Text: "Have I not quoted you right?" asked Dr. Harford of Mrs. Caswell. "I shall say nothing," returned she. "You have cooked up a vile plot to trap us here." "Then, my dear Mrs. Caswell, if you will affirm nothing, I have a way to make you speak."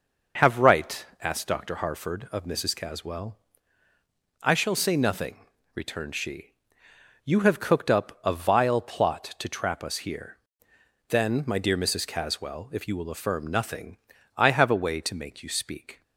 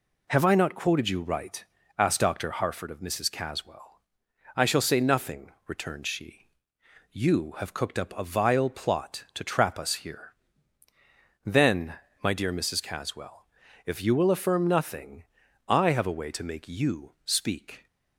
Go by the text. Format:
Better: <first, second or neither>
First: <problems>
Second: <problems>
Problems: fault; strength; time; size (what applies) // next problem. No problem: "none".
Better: second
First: skips "I not quoted you"; at 0.5 s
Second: none